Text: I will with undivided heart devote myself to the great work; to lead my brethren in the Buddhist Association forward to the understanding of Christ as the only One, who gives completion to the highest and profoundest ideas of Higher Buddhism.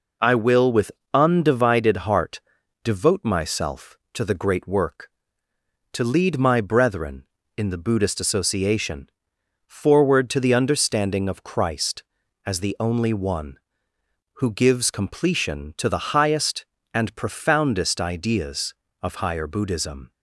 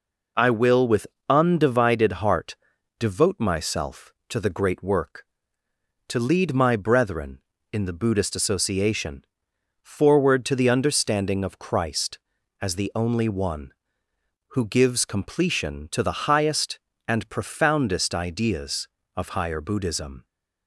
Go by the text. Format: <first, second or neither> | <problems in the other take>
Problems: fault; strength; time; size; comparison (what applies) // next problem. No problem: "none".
neither | pauses between "with" and "undivided"; slight; the same in both // pauses between "heart" and "devote"; the same in both // pauses between "Association" and "forward"; noticeable; the same in both